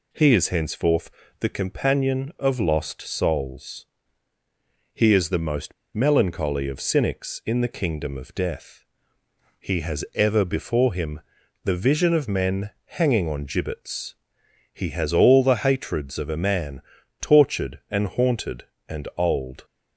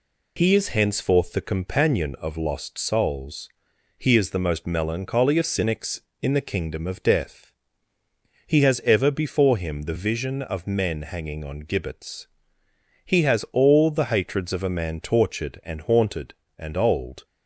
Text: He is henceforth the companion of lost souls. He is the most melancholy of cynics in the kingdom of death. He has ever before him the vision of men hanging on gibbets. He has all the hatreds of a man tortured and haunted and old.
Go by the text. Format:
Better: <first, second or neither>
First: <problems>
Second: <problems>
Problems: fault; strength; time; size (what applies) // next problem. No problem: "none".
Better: second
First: pauses between "henceforth" and "the"; slight; at 1.0 s; 0.30 s long // pauses between "most" and "melancholy"; slight; at 5.7 s; 0.21 s long // pauses between "him" and "the"; at 11.2 s; 0.44 s long // pauses between "man" and "tortured"; at 16.8 s; 0.40 s long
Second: none